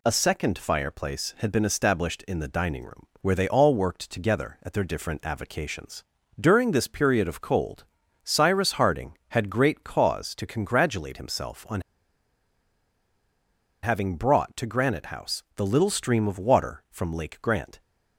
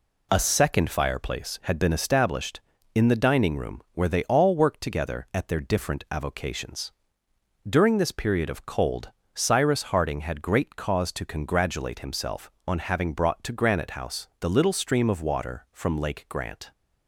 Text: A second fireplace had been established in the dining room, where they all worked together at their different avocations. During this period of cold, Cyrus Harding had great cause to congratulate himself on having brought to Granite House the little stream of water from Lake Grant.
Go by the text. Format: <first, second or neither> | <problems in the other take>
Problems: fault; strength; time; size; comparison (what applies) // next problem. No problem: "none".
second | pauses between "on" and "having"; strong; at 11.8 s; 2.0 s long